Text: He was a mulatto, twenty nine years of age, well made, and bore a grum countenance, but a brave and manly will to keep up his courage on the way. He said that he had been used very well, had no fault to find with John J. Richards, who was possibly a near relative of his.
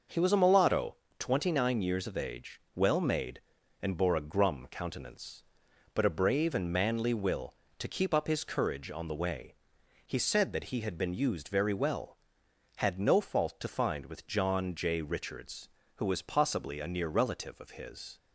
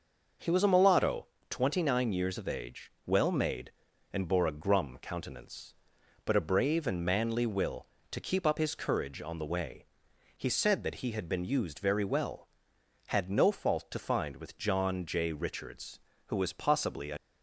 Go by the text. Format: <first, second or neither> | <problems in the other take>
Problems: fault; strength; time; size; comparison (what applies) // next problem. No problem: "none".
first | starts louder than the rest; noticeable; until 1.6 s; 6 dB; noticeable in the first // stops before "near relative of his"; at 17.1 s